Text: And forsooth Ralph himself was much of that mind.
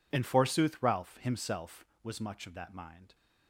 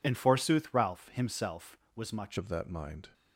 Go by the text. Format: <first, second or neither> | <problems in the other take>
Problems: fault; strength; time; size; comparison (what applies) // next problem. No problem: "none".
first | changes voice at "of"; from 2.3 s on; 0.7 s long